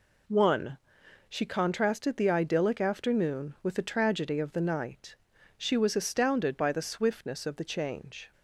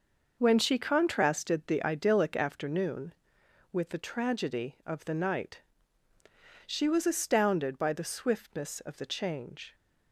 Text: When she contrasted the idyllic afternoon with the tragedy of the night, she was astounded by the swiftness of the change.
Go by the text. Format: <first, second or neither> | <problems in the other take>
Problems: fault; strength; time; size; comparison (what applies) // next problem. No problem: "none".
second | says "One" for "When"; at 0.2 s